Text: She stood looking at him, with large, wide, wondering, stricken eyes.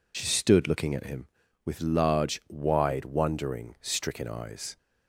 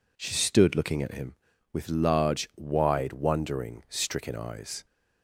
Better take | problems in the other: second | loses the start of "She"; at 0.1 s; 55 ms

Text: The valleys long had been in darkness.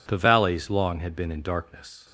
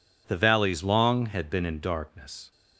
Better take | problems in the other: neither | none

